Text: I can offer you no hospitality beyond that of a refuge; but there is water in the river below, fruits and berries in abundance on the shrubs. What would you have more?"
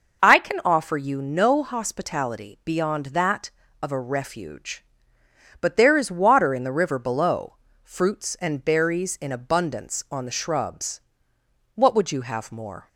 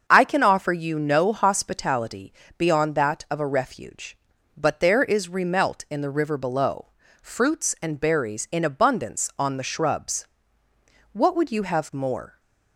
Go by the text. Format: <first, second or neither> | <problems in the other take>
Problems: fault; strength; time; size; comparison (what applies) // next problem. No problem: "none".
first | starts louder than the rest; until 1.0 s; 7 dB // pauses between "hospitality" and "beyond"; slight; at 2.3 s; 0.28 s long // says "remelt" for "water"; at 5.2 s